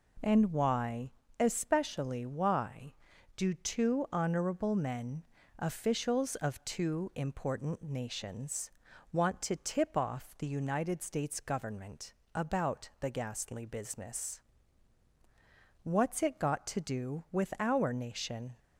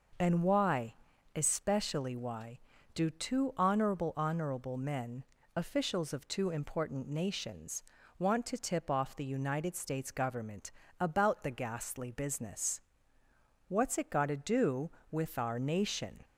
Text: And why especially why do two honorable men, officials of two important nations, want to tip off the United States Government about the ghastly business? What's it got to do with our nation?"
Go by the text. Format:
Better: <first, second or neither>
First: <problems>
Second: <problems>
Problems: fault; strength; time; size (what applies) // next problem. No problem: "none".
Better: first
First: pauses between "why" and "especially"; slight; at 1.1 s; 0.30 s long // pauses between "Government" and "about"; slight; at 12.1 s; 0.22 s long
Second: pauses between "why" and "especially"; at 0.9 s; 0.42 s long // says "honorable" twice; at 4.1 s // pauses between "Government" and "about"; slight; at 10.6 s; 0.30 s long